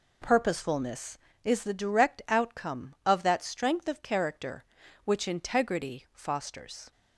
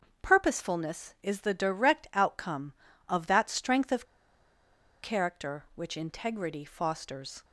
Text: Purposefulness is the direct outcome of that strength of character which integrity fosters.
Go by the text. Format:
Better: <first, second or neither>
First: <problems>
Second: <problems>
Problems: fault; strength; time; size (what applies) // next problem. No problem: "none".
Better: first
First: none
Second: starts louder than the rest; until 1.3 s; 6.5 dB // pauses between "of" and "character"; at 4.0 s; 0.99 s long